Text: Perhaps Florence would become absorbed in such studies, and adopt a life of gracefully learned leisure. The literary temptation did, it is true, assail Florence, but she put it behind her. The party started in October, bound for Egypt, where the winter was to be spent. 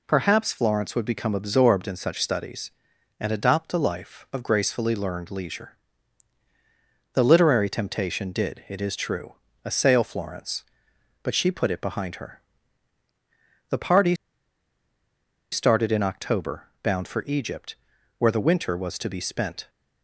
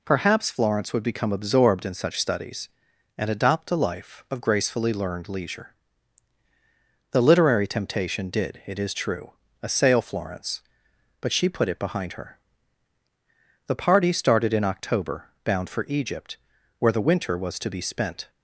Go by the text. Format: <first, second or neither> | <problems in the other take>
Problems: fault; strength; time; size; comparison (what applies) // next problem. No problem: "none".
second | pauses between "party" and "started"; strong; at 14.1 s; 1.3 s long